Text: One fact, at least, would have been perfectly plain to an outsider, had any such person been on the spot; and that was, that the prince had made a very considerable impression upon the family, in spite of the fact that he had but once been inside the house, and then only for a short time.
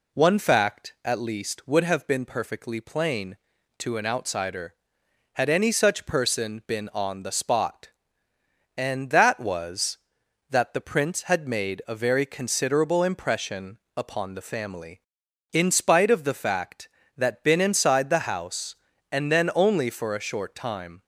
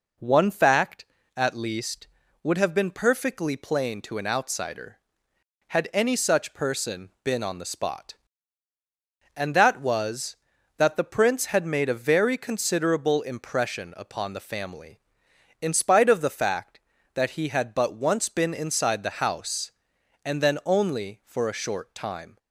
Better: second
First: pauses between "impression" and "upon"; slight; at 13.7 s; 0.18 s long // skips "he had but once"; at 17.4 s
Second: none

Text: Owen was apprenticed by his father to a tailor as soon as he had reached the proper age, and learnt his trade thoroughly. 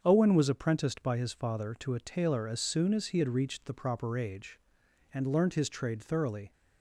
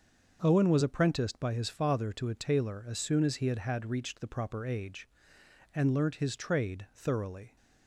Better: first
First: starts louder than the rest; strong; until 1.0 s; 7 dB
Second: starts louder than the rest; until 1.4 s; 6.5 dB // says "had" twice; at 3.5 s

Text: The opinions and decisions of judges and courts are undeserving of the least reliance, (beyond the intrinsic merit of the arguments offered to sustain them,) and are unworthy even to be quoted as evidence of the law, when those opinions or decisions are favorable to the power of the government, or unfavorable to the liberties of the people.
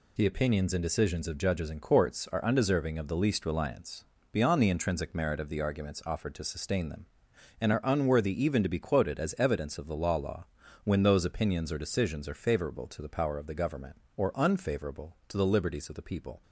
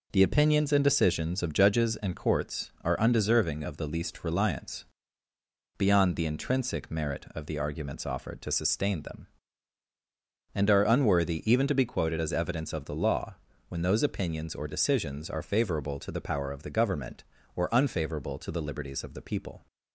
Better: second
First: says "law" twice; at 10.1 s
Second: none

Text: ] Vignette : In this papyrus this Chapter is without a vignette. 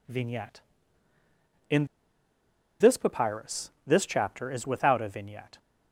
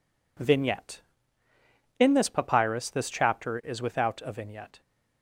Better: second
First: pauses between "In" and "this"; noticeable; at 1.8 s; 0.93 s long // pauses between "papyrus" and "this"; slight; at 3.6 s; 0.16 s long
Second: none

